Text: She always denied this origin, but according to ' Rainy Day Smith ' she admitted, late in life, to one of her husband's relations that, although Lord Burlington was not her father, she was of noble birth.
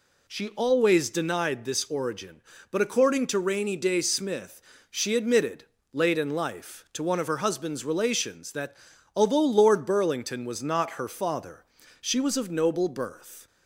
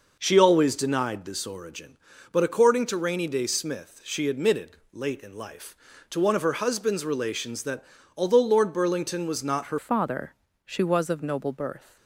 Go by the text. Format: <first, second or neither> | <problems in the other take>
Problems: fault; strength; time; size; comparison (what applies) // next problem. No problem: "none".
first | changes voice at "father"; from 9.7 s on; 2.2 s long